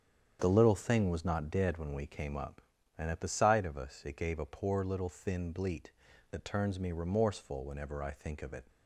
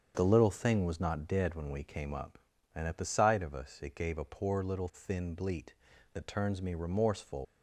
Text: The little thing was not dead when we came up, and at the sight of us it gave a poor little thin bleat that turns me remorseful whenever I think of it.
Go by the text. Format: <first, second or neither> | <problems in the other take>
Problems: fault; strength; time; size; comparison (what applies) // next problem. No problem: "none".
first | starts louder than the rest; strong; until 1.1 s; 7.5 dB; strong in the first // stops before "whenever I think of it"; at 7.4 s